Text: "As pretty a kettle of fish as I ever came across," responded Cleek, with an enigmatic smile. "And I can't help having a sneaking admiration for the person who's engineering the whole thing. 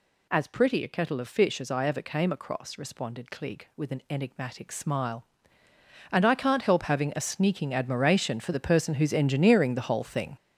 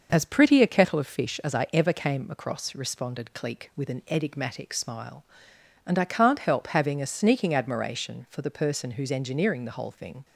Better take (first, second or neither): second